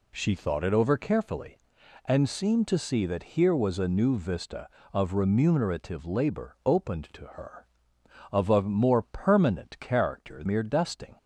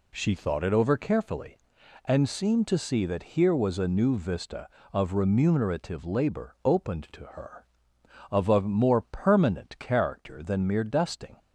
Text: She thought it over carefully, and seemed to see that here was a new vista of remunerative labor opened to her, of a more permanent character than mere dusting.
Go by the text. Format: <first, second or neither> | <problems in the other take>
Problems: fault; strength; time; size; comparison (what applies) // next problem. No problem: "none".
second | skips "than"; at 10.4 s